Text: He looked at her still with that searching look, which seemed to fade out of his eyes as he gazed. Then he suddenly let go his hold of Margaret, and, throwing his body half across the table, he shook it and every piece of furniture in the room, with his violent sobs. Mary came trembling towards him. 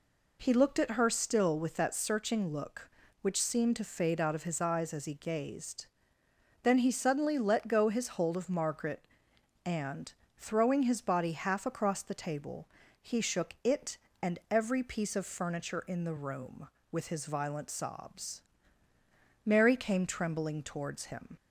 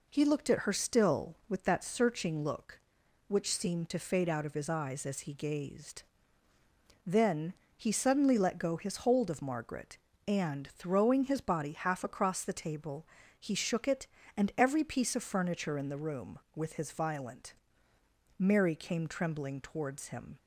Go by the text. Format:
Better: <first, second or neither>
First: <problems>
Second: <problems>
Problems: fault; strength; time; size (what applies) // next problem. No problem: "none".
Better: first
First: none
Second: pauses between "Then" and "he"; slight; at 7.5 s; 0.24 s long // skips "sobs"; at 17.9 s